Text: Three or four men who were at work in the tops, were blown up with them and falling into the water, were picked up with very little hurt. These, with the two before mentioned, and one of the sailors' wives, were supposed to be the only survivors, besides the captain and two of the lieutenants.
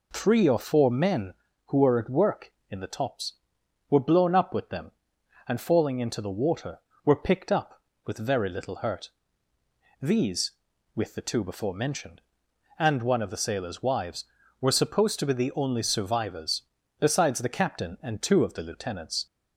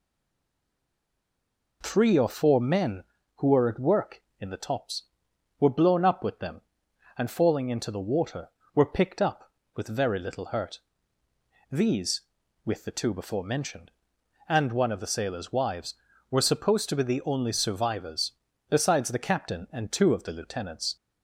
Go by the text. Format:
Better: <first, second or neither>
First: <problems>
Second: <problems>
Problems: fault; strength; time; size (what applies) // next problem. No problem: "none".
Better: first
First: none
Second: stays silent before the first word; noticeable; until 1.8 s; 1.8 s long